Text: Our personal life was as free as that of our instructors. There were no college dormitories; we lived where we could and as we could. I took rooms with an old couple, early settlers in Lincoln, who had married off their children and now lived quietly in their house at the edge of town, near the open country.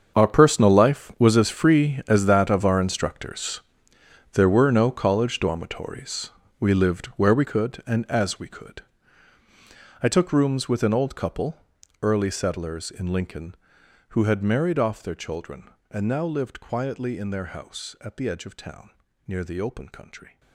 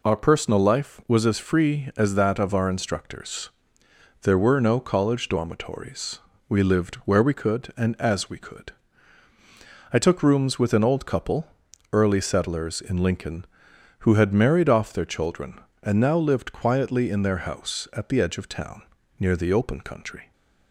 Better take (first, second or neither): second